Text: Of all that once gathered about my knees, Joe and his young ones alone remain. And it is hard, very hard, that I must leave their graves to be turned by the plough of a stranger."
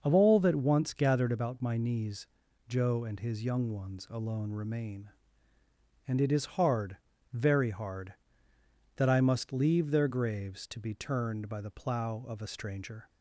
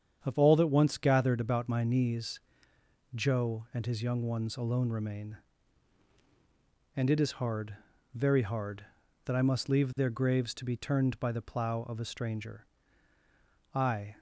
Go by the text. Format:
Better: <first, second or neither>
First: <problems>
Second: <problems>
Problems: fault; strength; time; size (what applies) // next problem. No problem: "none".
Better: first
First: starts louder than the rest; until 1.0 s; 6 dB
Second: starts louder than the rest; strong; until 1.2 s; 8 dB // goes on to say "I"; slight; from 13.7 s on; 0.44 s long